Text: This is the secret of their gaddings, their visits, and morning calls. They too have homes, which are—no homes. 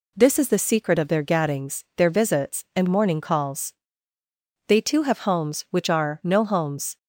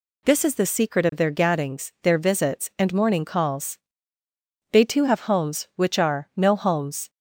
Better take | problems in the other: neither | none

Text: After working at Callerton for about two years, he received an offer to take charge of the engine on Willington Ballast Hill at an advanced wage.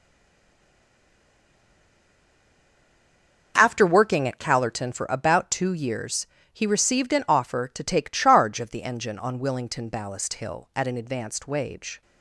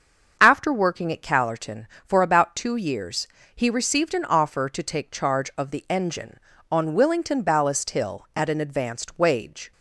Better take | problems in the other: second | stays silent before the first word; strong; until 3.5 s; 3.5 s long // starts louder than the rest; noticeable; until 4.5 s; 6 dB; also in the second

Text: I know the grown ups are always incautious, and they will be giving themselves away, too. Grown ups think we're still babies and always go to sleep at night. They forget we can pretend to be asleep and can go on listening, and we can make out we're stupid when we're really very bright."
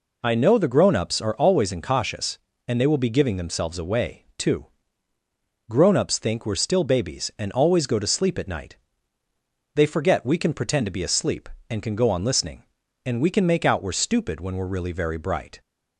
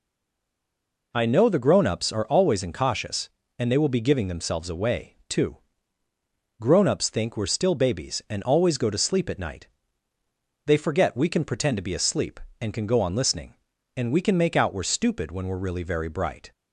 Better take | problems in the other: first | stays silent before the first word; until 1.1 s; 1.1 s long

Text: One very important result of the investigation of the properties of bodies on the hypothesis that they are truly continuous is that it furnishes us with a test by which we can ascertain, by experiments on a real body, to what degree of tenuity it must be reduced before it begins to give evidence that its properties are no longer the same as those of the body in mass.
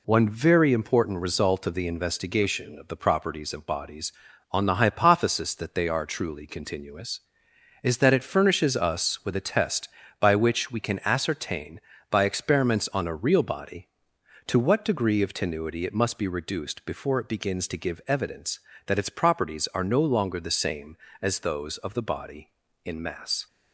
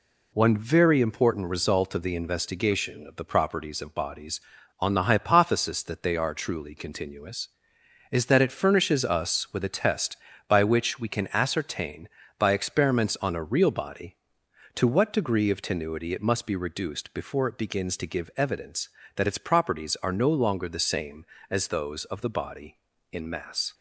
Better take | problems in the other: neither | none

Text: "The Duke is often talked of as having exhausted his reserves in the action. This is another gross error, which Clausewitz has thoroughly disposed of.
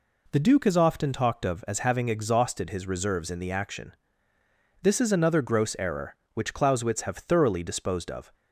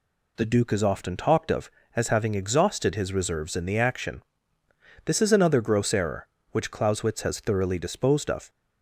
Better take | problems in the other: second | says "have" for "has"; at 7.0 s

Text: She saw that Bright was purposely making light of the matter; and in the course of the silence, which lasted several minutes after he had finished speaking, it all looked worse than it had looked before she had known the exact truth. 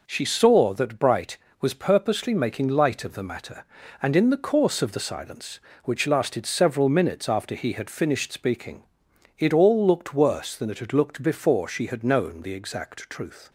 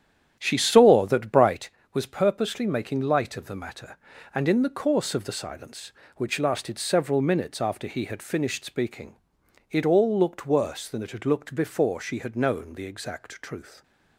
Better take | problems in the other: first | starts louder than the rest; strong; until 1.6 s; 10 dB

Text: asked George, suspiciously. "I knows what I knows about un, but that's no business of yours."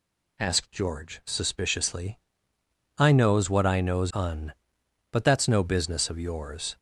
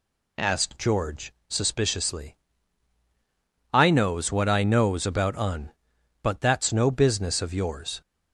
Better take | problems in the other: second | skips "about"; at 4.1 s

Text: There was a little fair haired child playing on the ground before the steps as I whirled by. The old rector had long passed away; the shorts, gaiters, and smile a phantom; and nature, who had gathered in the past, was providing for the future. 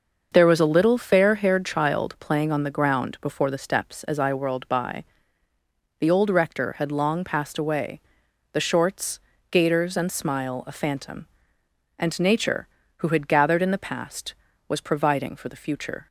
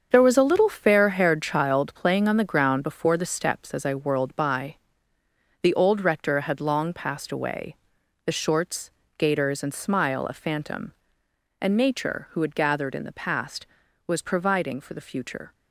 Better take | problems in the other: first | gets quieter; strong; throughout; 9.5 dB // starts louder than the rest; strong; until 1.1 s; 7 dB; also in the first

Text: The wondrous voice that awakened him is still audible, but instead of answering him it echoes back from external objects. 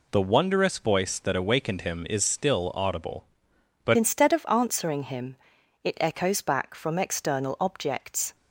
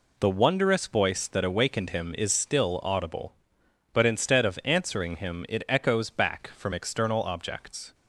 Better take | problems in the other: second | changes voice at "instead"; from 3.9 s on; 4.4 s long // pauses between "him" and "it"; noticeable; at 5.3 s; 0.48 s long

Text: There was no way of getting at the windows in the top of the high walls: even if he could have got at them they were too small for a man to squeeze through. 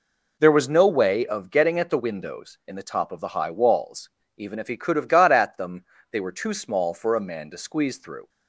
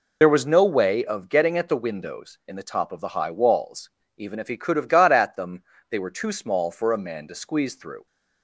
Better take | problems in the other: first | loses the start of "There"; at 0.2 s; 40 ms // pauses between "them" and "they"; slight; at 5.6 s; 0.28 s long; slight in the first

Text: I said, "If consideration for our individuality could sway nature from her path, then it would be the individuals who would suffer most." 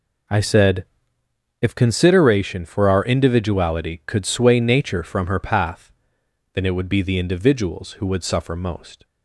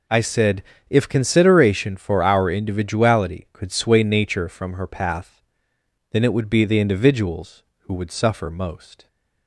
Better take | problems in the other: neither | none

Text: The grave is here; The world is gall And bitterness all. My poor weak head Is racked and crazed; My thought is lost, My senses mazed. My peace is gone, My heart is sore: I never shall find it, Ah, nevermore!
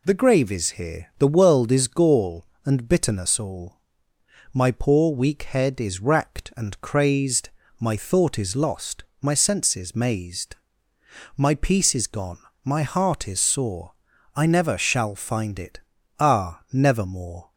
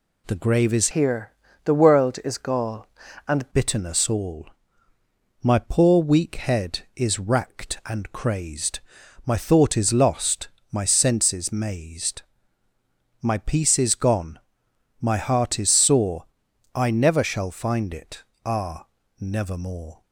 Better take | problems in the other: first | changes voice from "here" to "And"; from 0.9 to 3.4 s; 2.5 s long

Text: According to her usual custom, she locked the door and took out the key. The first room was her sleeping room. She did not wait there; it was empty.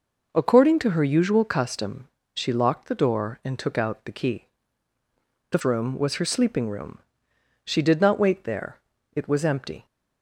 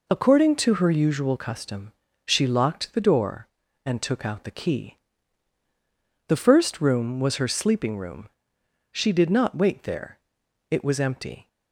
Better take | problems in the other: second | skips "first"; at 5.6 s

